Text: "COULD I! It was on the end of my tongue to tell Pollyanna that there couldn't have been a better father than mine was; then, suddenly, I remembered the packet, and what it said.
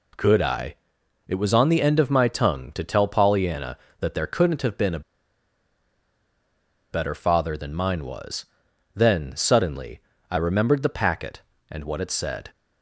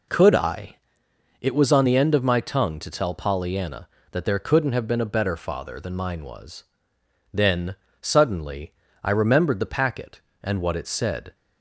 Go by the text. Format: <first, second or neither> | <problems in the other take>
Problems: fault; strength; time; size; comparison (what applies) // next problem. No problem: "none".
second | pauses between "a" and "better"; strong; at 5.0 s; 1.9 s long